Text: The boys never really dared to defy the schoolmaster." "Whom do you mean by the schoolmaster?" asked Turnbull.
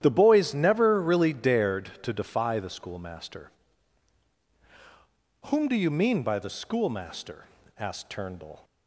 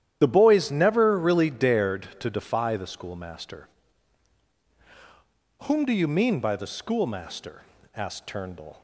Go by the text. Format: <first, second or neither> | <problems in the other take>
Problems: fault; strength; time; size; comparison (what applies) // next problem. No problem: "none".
first | loses the start of "The"; at 0.2 s; 30 ms // starts louder than the rest; strong; until 1.2 s; 10.5 dB; strong in the first